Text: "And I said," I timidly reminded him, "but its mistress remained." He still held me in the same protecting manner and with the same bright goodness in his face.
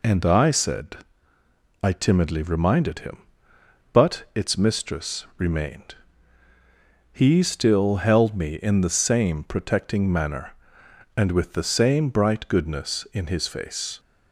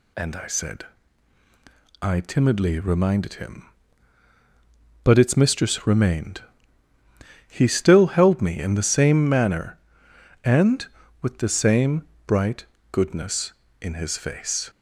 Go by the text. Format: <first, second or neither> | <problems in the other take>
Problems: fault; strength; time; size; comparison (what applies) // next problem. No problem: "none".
first | skips "protecting"; at 9.2 s // pauses between "same" and "bright"; slight; at 12.0 s; 0.24 s long // pauses between "bright" and "goodness"; slight; at 12.6 s; 0.28 s long